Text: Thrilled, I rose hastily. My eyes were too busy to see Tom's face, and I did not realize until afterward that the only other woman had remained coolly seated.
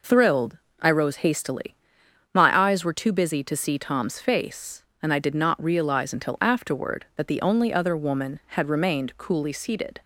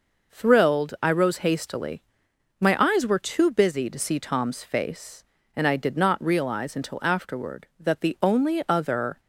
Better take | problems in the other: first | stops before "woman had remained coolly seated"; at 9.1 s

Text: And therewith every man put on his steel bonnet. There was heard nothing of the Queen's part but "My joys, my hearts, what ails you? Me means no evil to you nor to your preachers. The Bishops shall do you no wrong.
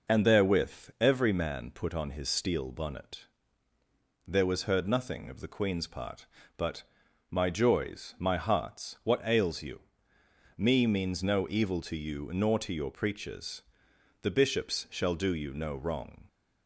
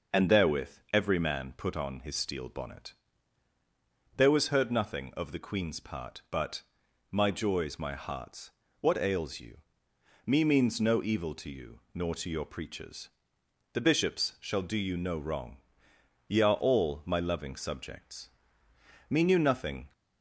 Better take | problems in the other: first | pauses between "therewith" and "every"; slight; at 0.7 s; 0.20 s long // pauses between "but" and "My"; noticeable; at 6.6 s; 0.46 s long; noticeable in the first // goes on to say "Ye are all my loving subjects Me knew nothing"; strong; from 16.2 s on; 3.6 s long

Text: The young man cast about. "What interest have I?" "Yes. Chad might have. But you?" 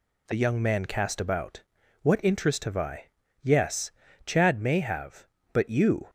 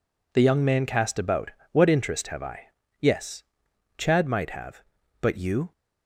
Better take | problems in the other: second | says "may" for "might"; at 4.5 s

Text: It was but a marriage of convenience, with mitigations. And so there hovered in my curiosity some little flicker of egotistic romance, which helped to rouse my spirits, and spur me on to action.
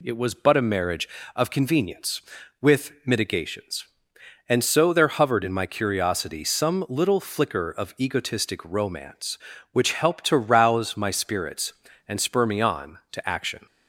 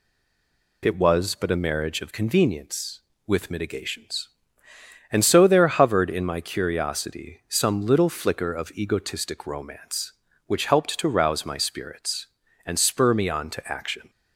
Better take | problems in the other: first | stays silent before the first word; slight; until 0.8 s; 0.8 s long

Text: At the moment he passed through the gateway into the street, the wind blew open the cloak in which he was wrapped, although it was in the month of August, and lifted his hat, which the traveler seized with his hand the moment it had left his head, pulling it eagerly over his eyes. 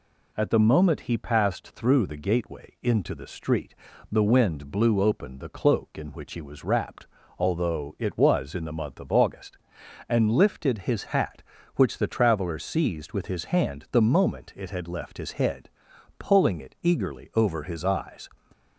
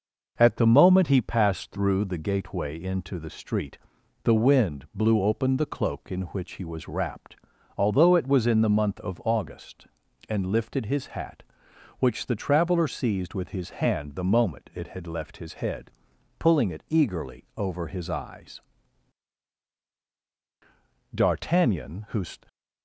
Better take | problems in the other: first | goes on to say "D'Artagnan who"; noticeable; from 21.1 s on; 1.1 s long

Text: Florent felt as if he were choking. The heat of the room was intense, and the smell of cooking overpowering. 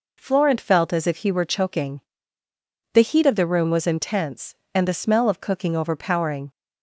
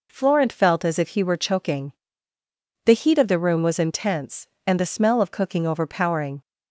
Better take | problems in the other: neither | none

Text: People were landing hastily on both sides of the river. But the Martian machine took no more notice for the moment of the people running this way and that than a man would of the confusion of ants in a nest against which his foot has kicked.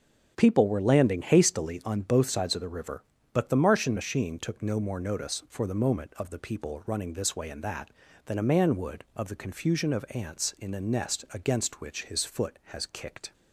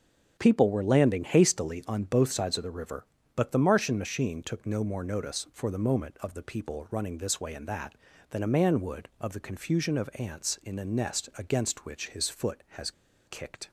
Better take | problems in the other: first | starts louder than the rest; strong; until 1.3 s; 7 dB; strong in the first // pauses between "has" and "kicked"; slight; at 12.9 s; 0.35 s long

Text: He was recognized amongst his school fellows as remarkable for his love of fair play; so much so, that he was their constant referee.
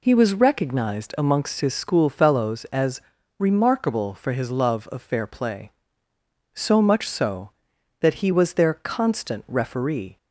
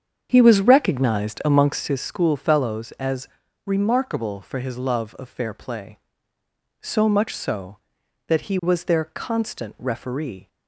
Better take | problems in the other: first | starts louder than the rest; strong; until 2.0 s; 7.5 dB // pauses between "as" and "remarkable"; at 3.2 s; 0.38 s long; also in the first

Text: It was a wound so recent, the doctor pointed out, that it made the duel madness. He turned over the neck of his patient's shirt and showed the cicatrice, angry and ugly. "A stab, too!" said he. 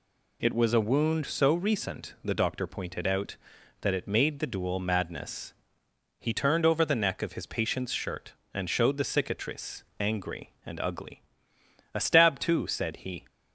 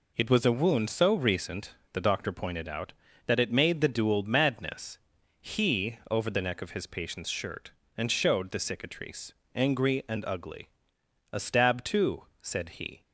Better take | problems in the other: first | skips "turned"; at 6.0 s

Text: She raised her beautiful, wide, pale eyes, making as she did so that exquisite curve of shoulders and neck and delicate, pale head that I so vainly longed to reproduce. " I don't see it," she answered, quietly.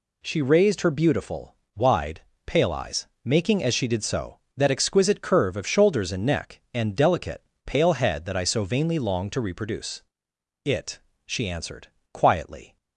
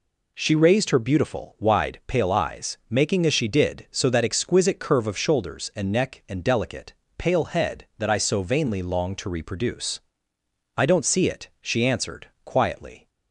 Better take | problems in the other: second | skips "I don't see"; at 10.6 s

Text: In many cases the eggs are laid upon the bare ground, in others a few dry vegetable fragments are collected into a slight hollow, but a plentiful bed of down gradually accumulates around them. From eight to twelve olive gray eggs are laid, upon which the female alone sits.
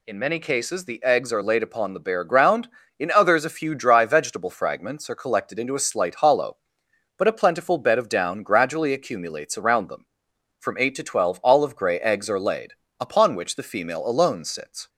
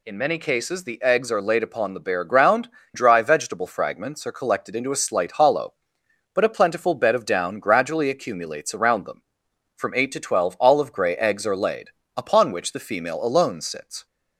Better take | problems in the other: first | skips "in others a few"; at 2.8 s

